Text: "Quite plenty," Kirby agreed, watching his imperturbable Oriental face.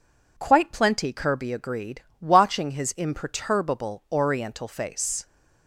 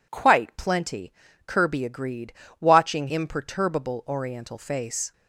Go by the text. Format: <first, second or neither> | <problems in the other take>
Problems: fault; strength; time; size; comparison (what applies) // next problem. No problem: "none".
first | skips "his"; at 3.0 s